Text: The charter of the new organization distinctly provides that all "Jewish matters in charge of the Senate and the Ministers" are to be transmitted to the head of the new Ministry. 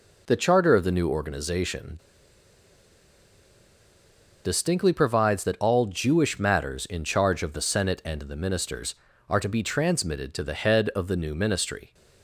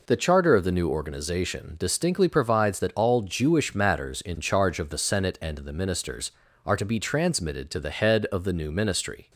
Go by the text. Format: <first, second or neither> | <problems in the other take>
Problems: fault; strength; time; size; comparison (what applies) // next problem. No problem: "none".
second | pauses between "organization" and "distinctly"; strong; at 1.9 s; 2.4 s long